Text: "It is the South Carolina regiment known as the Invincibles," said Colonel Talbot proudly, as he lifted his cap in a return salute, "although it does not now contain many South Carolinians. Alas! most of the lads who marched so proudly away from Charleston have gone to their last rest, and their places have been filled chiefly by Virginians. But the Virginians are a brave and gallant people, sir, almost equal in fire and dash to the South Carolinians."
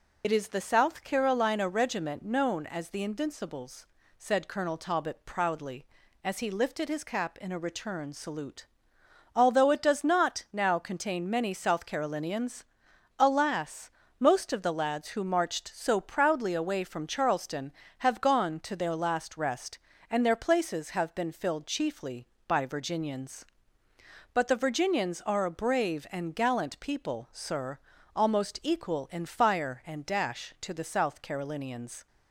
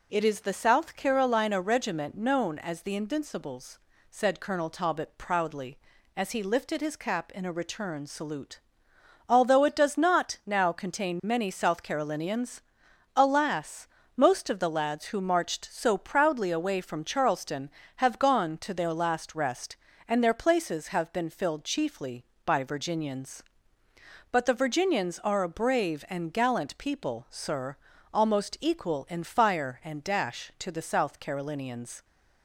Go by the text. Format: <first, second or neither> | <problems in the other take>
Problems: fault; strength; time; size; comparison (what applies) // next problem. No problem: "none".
second | loses the start of "It"; at 0.2 s; 65 ms